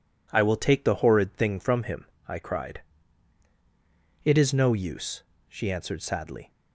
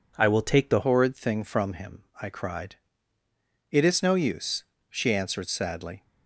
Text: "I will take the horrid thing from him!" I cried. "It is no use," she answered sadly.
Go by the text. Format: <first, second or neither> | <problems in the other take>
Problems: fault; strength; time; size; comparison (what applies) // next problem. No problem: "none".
first | changes voice at "horrid"; from 0.8 s on; 5.2 s long